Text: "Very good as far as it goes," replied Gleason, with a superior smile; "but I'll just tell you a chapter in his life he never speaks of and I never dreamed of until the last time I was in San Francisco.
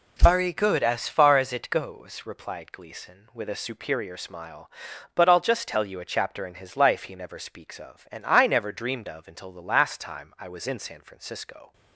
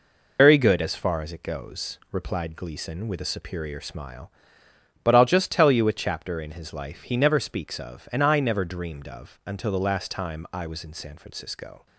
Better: first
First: none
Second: loses the start of "Very"; at 0.3 s; 105 ms

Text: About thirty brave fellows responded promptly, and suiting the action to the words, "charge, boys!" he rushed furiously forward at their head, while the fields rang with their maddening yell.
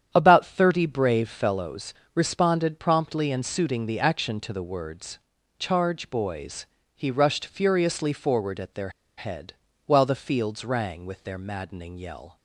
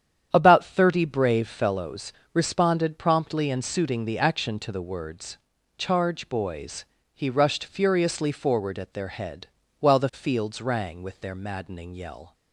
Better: second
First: starts louder than the rest; strong; until 1.1 s; 9 dB // pauses between "fellows" and "responded"; slight; at 1.9 s; 0.20 s long // pauses between "their" and "head"; slight; at 8.8 s; 0.27 s long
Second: starts louder than the rest; strong; until 1.3 s; 9 dB // pauses between "fellows" and "responded"; slight; at 2.1 s; 0.20 s long

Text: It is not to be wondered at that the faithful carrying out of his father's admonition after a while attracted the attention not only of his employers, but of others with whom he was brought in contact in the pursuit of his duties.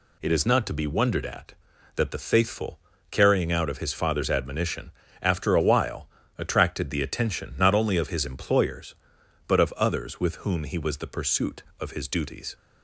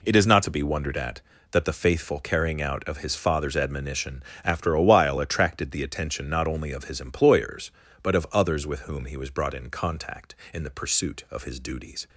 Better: second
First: pauses between "faithful" and "carrying"; slight; at 2.7 s; 0.32 s long // pauses between "admonition" and "after"; slight; at 4.9 s; 0.30 s long // pauses between "while" and "attracted"; slight; at 6.0 s; 0.30 s long // skips "brought in contact in"; at 10.9 s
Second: pauses between "admonition" and "after"; slight; at 4.2 s; 0.22 s long

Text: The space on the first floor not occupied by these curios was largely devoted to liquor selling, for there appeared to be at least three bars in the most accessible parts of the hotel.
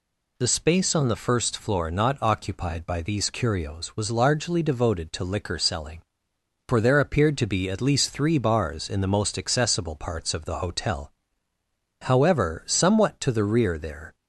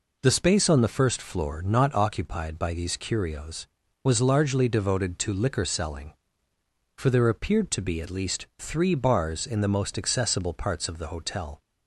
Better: second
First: goes on to say "However somewhat to the rear there"; strong; from 12.0 s on; 2.1 s long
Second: none

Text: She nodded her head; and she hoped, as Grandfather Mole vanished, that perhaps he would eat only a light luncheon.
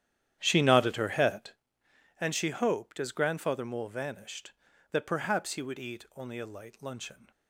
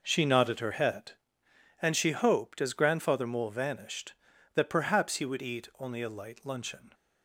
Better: second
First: starts louder than the rest; strong; until 1.6 s; 10.5 dB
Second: none

